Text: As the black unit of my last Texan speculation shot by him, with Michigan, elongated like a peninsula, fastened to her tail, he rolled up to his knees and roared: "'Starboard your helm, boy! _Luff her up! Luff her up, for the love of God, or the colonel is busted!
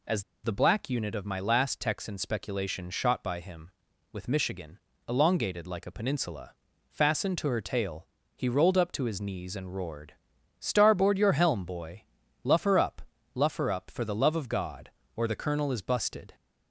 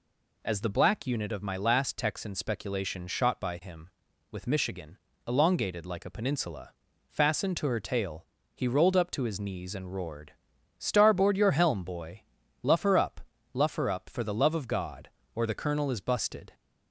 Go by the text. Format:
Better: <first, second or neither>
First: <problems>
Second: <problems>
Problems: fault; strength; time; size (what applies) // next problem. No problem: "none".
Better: second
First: pauses between "As" and "the"; slight; at 0.2 s; 0.21 s long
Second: none